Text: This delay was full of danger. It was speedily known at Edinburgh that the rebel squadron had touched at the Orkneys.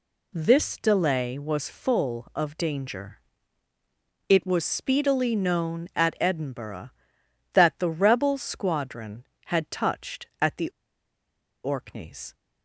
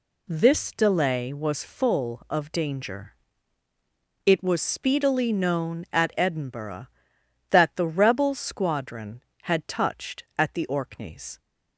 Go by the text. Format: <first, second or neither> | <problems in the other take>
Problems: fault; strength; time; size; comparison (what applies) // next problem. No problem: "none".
second | pauses between "the" and "Orkneys"; noticeable; at 10.7 s; 0.93 s long